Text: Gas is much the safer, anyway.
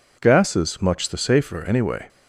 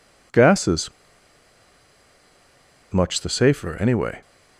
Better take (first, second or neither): first